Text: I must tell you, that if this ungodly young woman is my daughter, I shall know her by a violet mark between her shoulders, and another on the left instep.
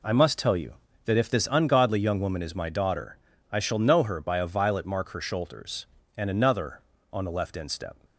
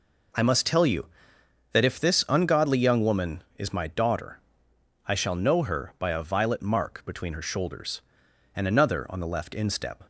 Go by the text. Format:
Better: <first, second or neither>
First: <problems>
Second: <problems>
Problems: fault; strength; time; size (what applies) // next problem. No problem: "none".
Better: second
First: skips "between"; at 5.0 s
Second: none